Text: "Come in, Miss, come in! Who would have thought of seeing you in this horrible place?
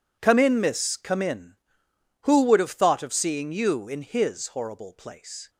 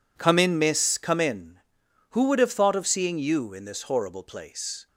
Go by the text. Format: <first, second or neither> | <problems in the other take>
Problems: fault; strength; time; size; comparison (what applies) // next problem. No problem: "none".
second | says "his" for "this"; at 4.0 s